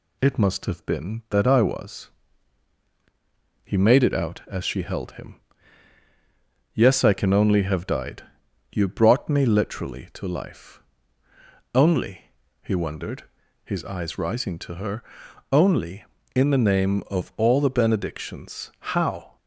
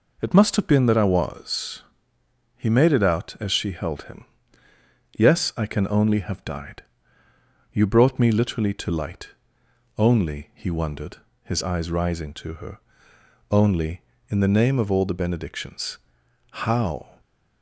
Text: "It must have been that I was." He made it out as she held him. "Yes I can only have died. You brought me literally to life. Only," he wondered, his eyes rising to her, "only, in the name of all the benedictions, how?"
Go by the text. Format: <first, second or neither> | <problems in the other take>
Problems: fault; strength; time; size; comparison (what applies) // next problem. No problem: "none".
first | says "light" for "life"; at 8.9 s